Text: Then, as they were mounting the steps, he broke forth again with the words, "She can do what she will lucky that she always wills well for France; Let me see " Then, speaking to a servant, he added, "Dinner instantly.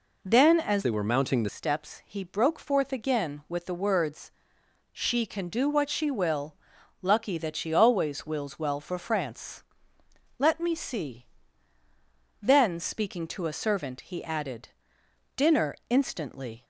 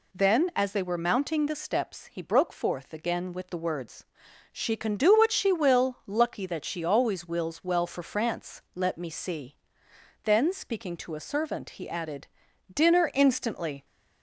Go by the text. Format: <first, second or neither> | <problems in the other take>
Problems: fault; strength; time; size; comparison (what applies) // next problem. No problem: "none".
second | changes voice from "they" to "the"; from 0.8 to 1.4 s; 0.6 s long // pauses between "will" and "lucky"; noticeable; at 6.5 s; 0.50 s long // pauses between "Dinner" and "instantly"; slight; at 15.7 s; 0.16 s long